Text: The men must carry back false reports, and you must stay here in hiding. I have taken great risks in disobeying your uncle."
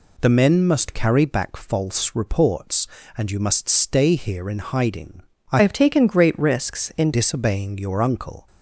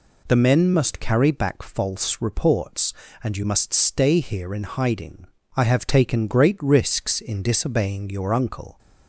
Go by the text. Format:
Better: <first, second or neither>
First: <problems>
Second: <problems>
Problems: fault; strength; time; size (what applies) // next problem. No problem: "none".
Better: second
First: changes voice from "have" to "in"; from 5.6 to 7.1 s; 1.5 s long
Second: none